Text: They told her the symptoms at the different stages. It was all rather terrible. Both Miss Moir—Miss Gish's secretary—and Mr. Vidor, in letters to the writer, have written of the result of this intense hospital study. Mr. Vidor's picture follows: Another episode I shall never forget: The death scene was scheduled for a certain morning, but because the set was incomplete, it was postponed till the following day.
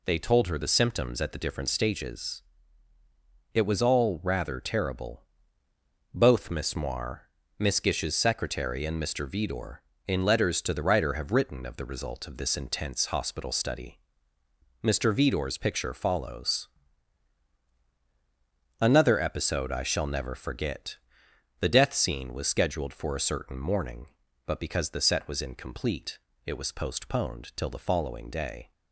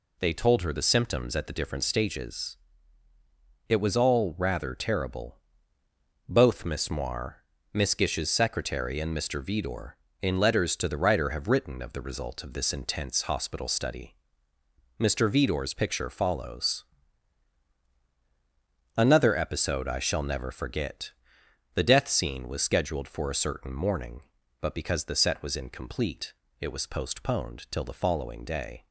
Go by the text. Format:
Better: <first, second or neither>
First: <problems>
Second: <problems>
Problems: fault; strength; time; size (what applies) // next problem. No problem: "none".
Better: neither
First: none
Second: none